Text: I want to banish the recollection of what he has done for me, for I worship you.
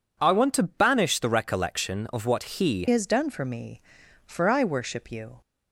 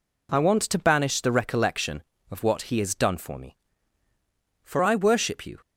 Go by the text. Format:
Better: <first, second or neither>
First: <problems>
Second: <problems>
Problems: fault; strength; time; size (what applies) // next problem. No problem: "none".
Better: second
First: changes voice at "has"; from 2.9 s on; 2.5 s long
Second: none